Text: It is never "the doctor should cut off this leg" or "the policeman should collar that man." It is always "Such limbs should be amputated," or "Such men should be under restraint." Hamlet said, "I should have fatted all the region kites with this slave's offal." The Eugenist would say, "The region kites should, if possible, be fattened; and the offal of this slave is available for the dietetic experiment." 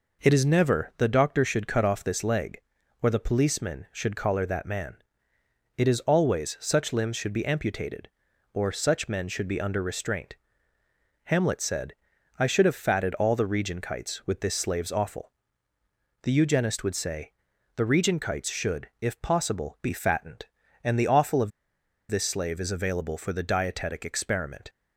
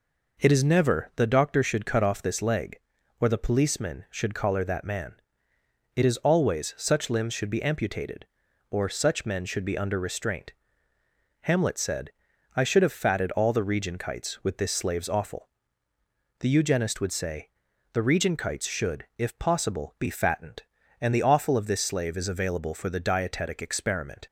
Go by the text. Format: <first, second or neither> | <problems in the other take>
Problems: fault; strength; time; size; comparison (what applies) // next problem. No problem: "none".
second | pauses between "of" and "this"; noticeable; at 21.5 s; 0.60 s long